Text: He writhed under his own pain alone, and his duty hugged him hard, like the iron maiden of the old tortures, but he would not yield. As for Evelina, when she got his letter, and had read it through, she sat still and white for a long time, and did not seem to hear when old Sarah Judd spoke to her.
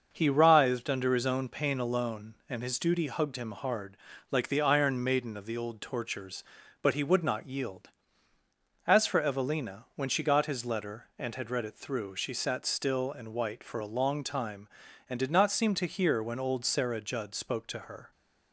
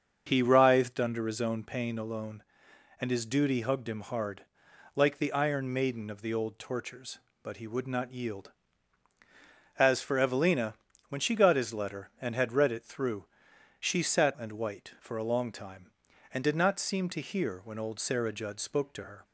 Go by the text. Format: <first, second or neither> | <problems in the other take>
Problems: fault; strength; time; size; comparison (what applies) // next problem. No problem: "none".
first | starts louder than the rest; until 1.2 s; 7 dB; also in the first // skips "still"; at 14.3 s